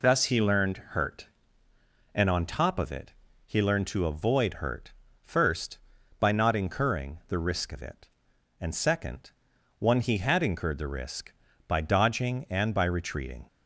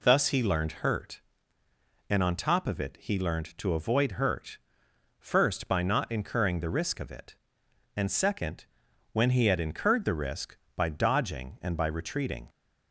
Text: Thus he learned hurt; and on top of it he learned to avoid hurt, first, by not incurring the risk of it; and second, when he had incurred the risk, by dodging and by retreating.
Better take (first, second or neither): second